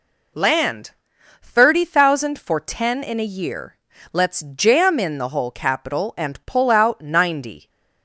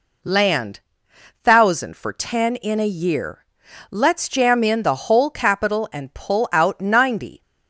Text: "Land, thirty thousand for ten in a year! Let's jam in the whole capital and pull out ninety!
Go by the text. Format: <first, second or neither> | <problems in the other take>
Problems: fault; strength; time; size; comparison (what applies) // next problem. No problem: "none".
first | skips "thirty"; at 1.1 s